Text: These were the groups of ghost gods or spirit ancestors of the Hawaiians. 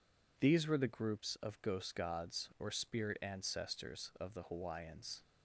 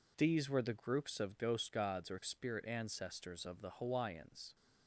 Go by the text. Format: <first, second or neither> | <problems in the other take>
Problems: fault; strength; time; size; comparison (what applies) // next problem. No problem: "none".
neither | none